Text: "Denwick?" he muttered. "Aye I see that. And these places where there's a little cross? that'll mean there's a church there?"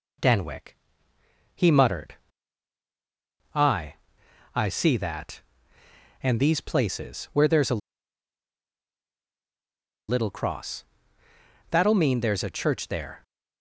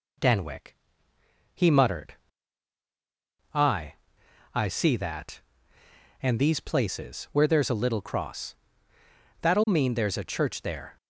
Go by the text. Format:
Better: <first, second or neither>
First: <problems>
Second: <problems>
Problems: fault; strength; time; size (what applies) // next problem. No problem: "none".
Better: second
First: pauses between "Aye" and "I"; noticeable; at 3.9 s; 0.58 s long // pauses between "a" and "little"; strong; at 7.8 s; 2.3 s long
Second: pauses between "Aye" and "I"; noticeable; at 3.9 s; 0.58 s long